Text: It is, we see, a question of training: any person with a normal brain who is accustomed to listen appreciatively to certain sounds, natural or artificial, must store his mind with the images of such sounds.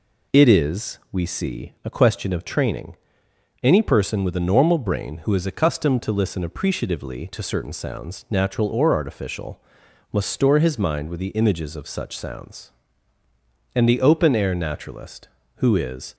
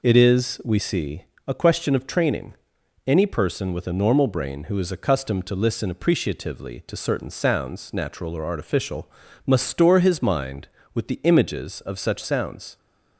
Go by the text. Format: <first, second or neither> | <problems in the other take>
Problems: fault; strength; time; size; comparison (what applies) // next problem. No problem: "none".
second | goes on to say "And the open air naturalist who is"; strong; from 13.7 s on; 2.4 s long